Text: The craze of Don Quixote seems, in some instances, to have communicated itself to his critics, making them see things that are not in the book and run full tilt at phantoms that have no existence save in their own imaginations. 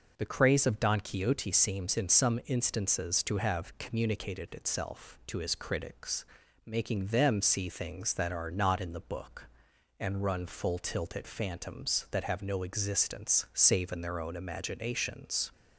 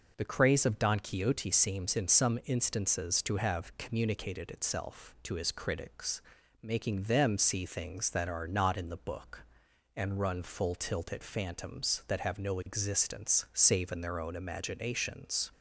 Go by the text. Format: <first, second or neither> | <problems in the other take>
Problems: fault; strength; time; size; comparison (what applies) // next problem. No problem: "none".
neither | none